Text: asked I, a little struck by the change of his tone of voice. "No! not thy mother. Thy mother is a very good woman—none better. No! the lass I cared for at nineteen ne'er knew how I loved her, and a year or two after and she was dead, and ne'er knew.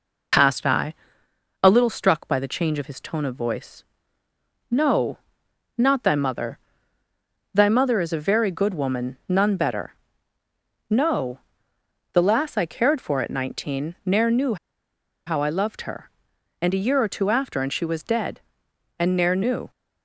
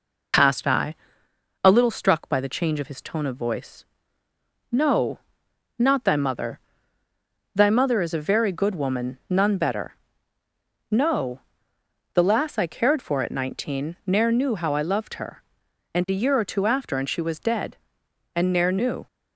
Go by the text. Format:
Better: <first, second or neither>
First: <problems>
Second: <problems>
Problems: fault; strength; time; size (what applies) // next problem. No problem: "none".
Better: second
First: pauses between "knew" and "how"; noticeable; at 14.5 s; 0.70 s long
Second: none